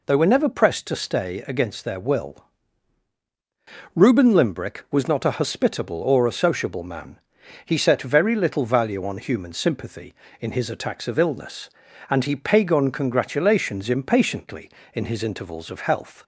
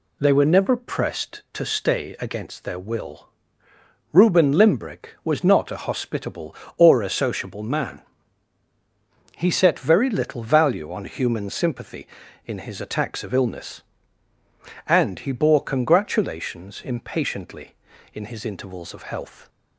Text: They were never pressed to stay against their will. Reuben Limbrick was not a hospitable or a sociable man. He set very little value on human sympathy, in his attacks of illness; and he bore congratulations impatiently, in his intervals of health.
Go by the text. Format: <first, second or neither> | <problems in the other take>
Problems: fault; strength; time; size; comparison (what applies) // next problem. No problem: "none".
second | says "pagon" for "bore"; at 12.3 s